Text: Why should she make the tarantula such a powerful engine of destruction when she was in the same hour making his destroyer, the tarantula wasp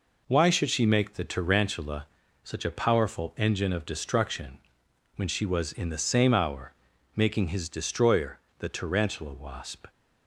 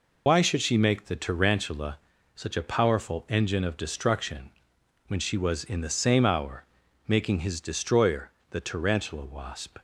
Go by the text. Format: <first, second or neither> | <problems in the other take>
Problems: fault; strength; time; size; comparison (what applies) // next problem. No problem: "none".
first | loses the start of "Why"; at 0.2 s; 80 ms // pauses between "tarantula" and "such"; slight; at 1.9 s; 0.36 s long; slight in the first // pauses between "destruction" and "when"; noticeable; at 4.5 s; 0.58 s long; noticeable in the first // pauses between "hour" and "making"; at 6.6 s; 0.42 s long; also in the first